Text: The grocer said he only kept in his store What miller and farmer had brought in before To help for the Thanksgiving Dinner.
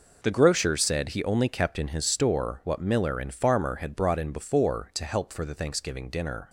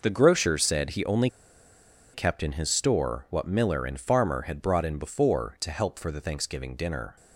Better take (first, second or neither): first